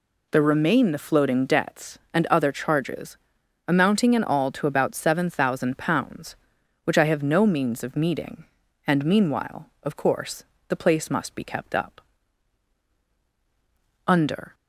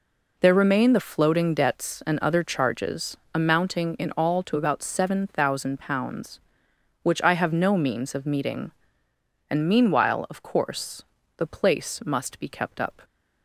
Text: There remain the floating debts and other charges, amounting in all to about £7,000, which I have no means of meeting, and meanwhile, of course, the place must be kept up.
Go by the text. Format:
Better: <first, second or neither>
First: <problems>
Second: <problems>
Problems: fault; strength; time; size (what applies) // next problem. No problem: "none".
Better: second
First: goes on to say "Under"; slight; from 14.0 s on; 0.48 s long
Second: none